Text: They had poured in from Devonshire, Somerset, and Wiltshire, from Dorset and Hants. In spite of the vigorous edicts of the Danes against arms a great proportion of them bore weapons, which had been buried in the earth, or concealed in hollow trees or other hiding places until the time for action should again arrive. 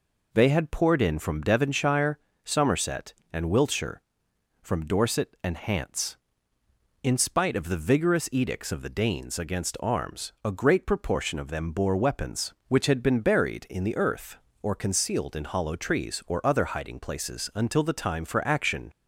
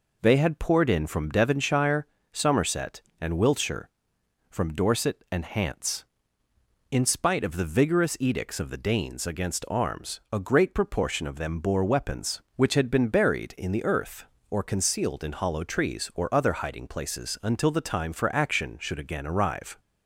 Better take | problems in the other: second | stops before "should again arrive"; at 18.9 s

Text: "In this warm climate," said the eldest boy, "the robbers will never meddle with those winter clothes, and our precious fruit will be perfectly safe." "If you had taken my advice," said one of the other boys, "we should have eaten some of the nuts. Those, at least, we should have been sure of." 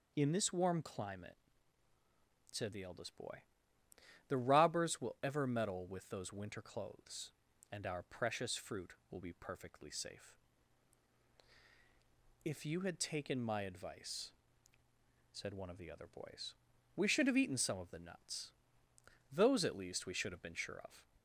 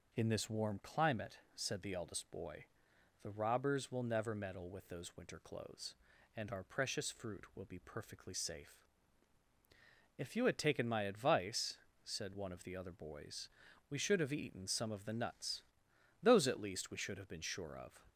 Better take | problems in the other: second | says "ever" for "never"; at 5.2 s

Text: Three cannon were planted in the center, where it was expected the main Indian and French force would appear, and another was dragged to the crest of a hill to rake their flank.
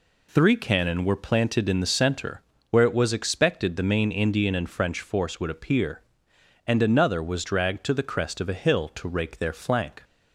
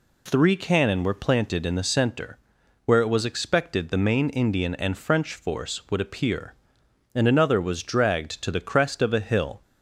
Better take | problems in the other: first | stops before "to rake their flank"; at 9.6 s

